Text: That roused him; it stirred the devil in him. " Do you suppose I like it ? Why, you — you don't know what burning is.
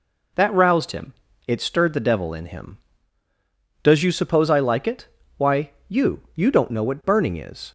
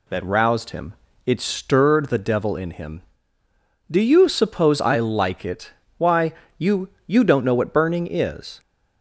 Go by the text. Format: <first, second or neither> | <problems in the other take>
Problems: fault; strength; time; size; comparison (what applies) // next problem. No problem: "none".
second | says "Does" for "Do"; at 3.8 s